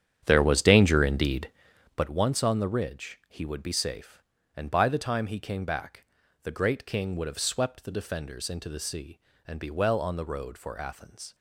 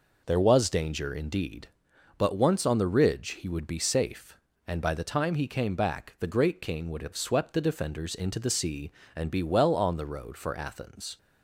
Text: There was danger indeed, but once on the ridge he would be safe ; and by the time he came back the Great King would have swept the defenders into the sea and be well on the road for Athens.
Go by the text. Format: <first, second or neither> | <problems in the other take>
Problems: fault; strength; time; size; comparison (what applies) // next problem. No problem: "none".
second | starts louder than the rest; strong; until 2.1 s; 9.5 dB // pauses between "back" and "the"; at 6.0 s; 0.38 s long